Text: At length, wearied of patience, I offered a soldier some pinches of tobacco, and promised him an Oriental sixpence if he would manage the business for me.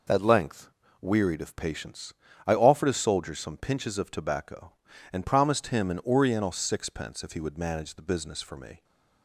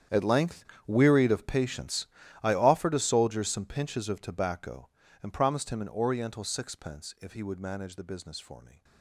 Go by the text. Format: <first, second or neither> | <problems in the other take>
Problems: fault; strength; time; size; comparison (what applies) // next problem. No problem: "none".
first | gets quieter; strong; throughout; 18.5 dB